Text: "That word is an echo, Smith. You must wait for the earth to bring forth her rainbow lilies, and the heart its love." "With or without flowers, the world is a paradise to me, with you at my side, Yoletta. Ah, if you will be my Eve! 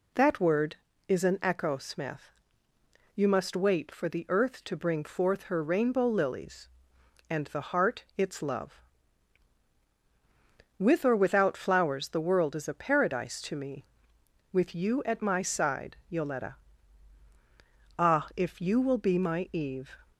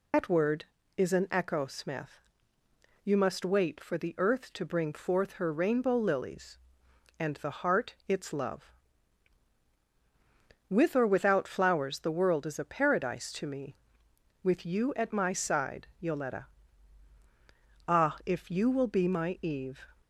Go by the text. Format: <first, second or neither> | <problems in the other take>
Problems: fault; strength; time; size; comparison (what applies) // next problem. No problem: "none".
first | loses the start of "That"; at 0.1 s; 115 ms